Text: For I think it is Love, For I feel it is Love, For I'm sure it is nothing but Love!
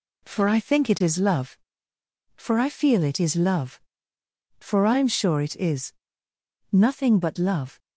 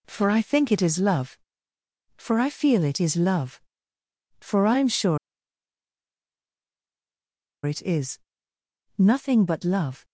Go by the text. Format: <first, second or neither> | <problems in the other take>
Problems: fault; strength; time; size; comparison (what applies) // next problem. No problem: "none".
first | pauses between "sure" and "it"; strong; at 5.1 s; 2.4 s long // pauses between "is" and "nothing"; noticeable; at 8.1 s; 0.80 s long; noticeable in the first